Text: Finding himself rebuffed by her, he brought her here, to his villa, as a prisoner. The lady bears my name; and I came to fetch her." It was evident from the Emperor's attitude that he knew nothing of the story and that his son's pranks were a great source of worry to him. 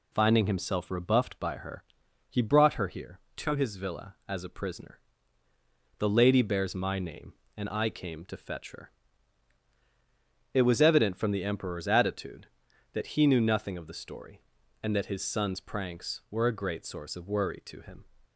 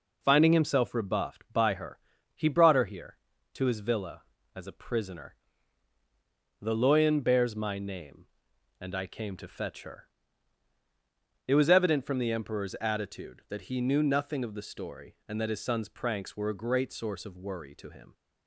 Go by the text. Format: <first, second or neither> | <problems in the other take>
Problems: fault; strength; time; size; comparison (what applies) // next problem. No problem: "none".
first | says "loyan" for "lady"; at 6.7 s